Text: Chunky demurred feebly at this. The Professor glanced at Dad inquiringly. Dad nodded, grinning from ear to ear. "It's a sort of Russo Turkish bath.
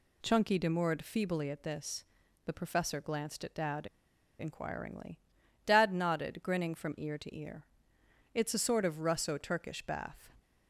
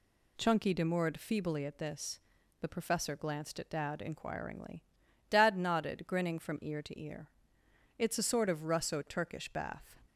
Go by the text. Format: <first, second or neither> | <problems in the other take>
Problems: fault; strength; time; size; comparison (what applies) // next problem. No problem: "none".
second | pauses between "Dad" and "inquiringly"; noticeable; at 3.8 s; 0.51 s long